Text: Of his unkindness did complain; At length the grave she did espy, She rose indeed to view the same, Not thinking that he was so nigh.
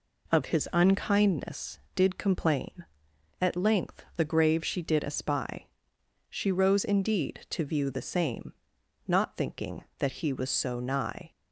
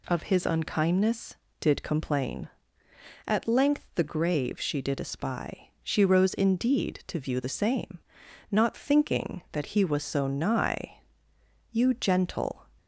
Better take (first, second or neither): first